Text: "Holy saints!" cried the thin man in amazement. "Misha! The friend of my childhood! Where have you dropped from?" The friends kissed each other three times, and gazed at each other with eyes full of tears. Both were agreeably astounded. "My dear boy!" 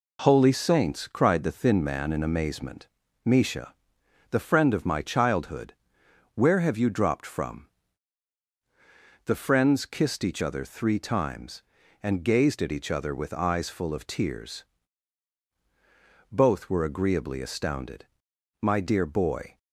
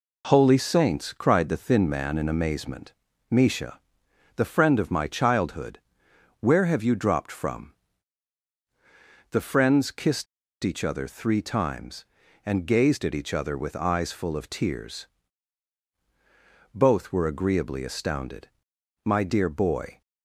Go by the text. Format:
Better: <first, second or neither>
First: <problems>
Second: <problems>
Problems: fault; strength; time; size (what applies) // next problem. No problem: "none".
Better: first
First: none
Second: pauses between "kissed" and "each"; at 10.2 s; 0.37 s long